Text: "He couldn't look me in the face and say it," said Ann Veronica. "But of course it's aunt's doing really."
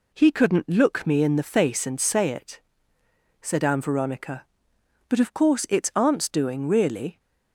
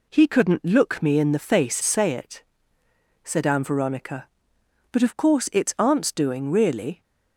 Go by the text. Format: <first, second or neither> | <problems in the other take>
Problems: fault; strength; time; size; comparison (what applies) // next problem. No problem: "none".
first | skips "and"; at 1.8 s